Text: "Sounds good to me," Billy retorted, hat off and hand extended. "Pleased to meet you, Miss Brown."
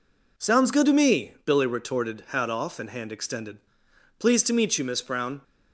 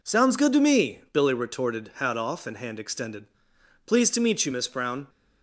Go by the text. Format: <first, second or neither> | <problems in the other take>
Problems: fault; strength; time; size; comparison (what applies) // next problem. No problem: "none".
neither | none